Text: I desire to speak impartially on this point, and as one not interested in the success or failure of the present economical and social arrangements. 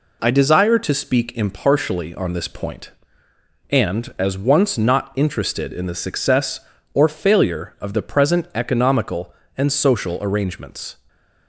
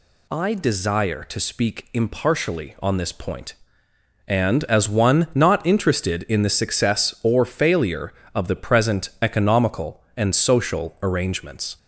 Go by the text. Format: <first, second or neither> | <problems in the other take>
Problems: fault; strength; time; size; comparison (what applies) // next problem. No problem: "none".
second | says "once" for "one"; at 4.3 s